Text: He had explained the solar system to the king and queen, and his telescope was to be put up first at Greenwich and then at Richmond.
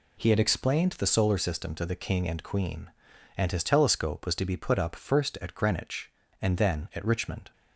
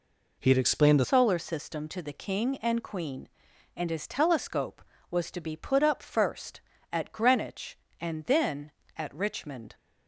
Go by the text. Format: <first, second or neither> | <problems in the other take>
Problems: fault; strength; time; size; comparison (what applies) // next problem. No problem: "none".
first | changes voice at "solar"; from 1.0 s on; 8.7 s long